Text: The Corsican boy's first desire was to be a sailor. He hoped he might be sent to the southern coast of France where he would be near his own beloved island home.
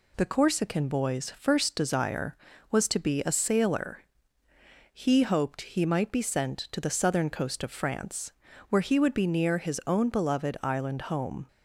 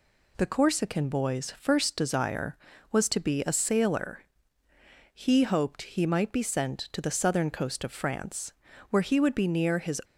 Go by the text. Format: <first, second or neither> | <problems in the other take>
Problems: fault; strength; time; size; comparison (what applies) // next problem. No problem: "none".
first | pauses between "France" and "where"; at 8.5 s; 0.38 s long; also in the first // stops before "own beloved island home"; at 10.0 s